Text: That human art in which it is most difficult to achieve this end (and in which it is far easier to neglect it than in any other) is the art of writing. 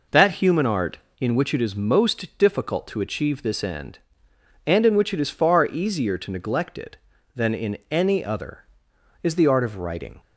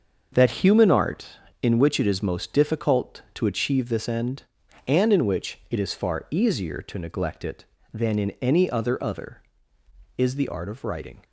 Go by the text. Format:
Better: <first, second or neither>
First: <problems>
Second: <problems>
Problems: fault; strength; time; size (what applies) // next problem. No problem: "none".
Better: first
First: none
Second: starts louder than the rest; until 1.3 s; 6.5 dB // says "other" twice; at 9.0 s